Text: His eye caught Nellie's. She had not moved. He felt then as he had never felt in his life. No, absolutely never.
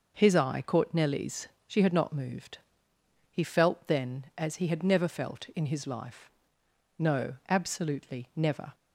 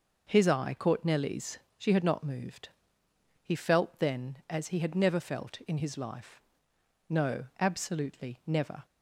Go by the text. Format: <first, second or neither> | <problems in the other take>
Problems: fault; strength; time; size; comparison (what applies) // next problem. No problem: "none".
neither | none